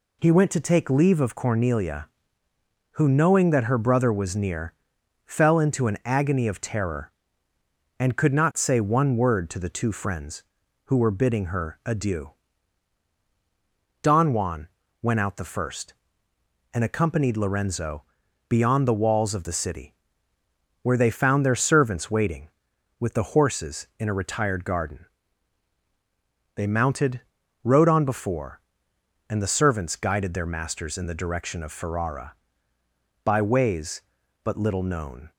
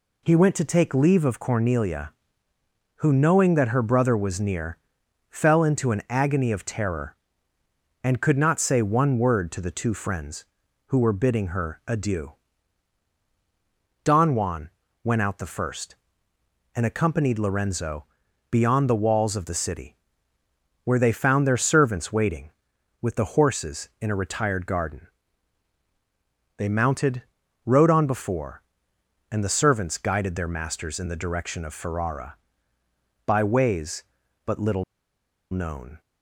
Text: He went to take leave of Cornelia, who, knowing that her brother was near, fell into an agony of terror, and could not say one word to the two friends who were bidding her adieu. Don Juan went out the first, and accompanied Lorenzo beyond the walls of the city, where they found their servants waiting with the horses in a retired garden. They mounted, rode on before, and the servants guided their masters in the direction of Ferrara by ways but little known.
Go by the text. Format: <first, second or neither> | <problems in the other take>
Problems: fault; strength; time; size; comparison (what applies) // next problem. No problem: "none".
first | pauses between "Juan" and "went"; slight; at 14.6 s; 0.34 s long; slight in the first // pauses between "Lorenzo" and "beyond"; at 18.0 s; 0.44 s long; also in the first // pauses between "little" and "known"; noticeable; at 34.8 s; 0.68 s long